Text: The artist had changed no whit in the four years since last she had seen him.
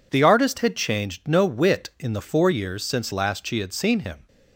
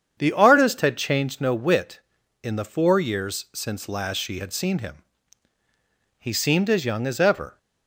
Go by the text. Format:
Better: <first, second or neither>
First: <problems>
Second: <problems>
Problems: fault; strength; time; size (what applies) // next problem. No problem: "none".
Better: first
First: none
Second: starts louder than the rest; strong; until 1.2 s; 8 dB // goes on to say "He seemed as young as ever"; from 6.1 s on; 1.4 s long